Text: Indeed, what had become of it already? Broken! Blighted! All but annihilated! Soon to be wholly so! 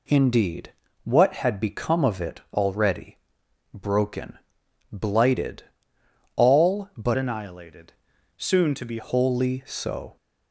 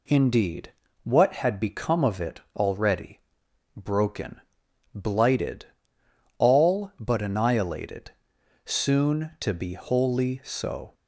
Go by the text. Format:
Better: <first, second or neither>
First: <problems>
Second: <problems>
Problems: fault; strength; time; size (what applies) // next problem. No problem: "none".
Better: second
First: changes voice from "annihilated" to "be"; from 7.1 to 8.9 s; 1.8 s long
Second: none